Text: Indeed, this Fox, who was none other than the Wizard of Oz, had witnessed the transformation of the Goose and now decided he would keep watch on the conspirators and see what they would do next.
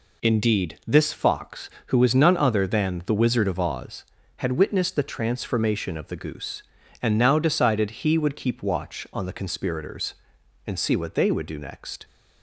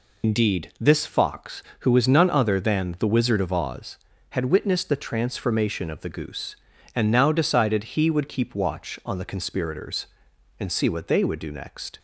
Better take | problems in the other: first | loses the start of "Indeed"; at 0.2 s; 90 ms

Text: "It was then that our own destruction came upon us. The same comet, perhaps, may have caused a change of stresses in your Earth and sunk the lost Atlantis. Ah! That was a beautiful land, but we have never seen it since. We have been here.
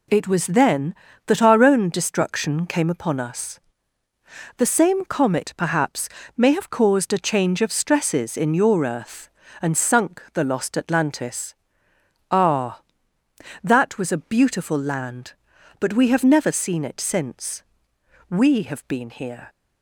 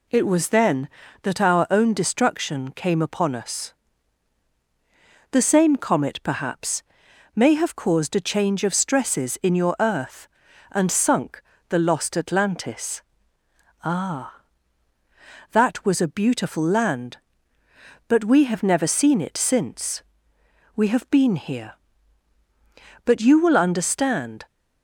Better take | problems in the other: first | pauses between "sunk" and "the"; slight; at 11.4 s; 0.28 s long // goes on to say "But you will understand"; from 23.0 s on; 1.4 s long

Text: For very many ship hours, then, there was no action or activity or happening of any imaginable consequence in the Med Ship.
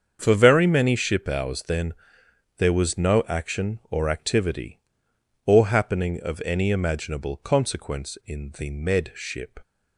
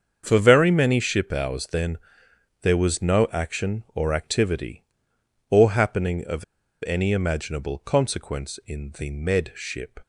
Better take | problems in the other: first | starts louder than the rest; until 1.2 s; 7 dB; strong in the first // pauses between "of" and "any"; at 6.4 s; 0.41 s long

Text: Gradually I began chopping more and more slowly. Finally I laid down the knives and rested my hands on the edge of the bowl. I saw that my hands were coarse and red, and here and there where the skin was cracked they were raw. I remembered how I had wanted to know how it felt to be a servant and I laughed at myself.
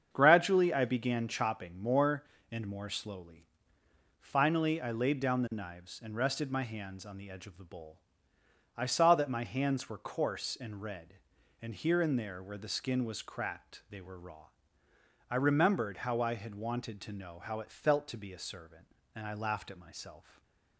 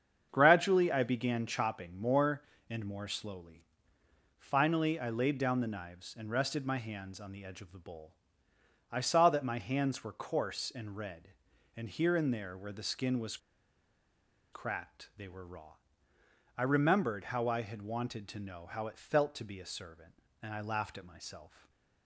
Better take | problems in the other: first | starts louder than the rest; strong; until 1.3 s; 7.5 dB; strong in the first // pauses between "was" and "cracked"; at 13.3 s; 1.1 s long // stays silent after the last word; slight; from 21.4 s on; 0.6 s long; slight in the first

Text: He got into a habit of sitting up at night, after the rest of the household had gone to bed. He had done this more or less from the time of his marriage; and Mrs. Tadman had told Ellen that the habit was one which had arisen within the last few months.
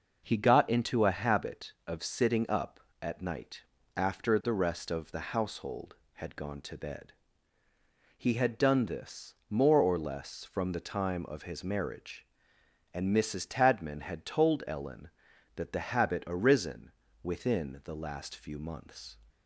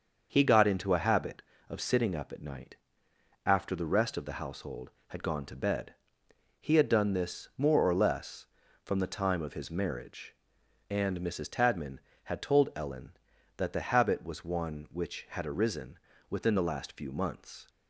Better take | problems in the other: second | starts louder than the rest; noticeable; until 1.3 s; 6 dB; also in the second // skips "was one which had"; at 16.2 s // pauses between "arisen" and "within"; slight; at 16.9 s; 0.32 s long; slight in the second

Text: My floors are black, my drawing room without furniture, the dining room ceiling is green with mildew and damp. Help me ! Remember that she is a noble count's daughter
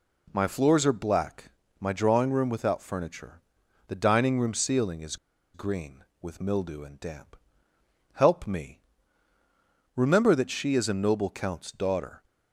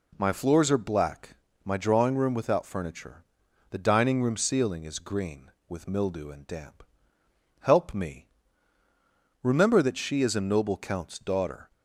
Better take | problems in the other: second | pauses between "is" and "green"; at 5.1 s; 0.37 s long

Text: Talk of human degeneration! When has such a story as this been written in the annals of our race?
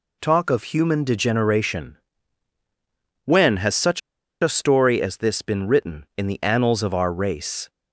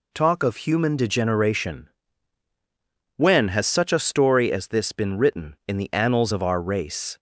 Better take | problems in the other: second | pauses between "such" and "a"; at 4.0 s; 0.41 s long

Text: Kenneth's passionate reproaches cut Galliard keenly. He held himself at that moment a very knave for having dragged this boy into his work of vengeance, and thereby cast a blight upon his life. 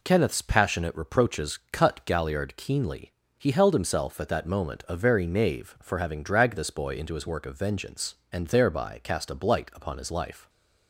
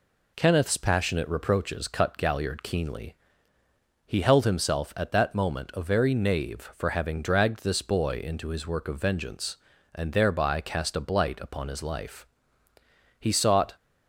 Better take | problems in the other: first | goes on to say "He sought"; from 13.1 s on; 0.56 s long

